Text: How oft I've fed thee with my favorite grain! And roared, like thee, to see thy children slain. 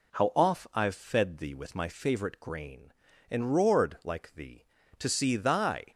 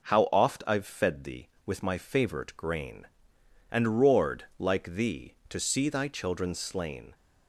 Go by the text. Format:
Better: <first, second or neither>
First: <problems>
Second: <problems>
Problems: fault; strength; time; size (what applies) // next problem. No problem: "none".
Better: second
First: stops before "children slain"; at 5.9 s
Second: none